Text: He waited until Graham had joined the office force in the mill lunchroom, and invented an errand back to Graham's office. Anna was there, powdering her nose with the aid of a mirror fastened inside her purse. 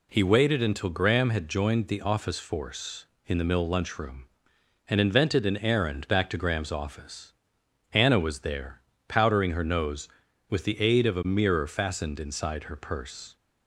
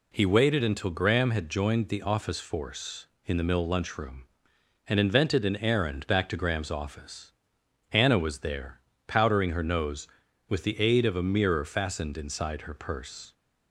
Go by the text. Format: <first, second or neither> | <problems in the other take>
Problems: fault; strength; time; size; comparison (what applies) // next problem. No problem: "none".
neither | none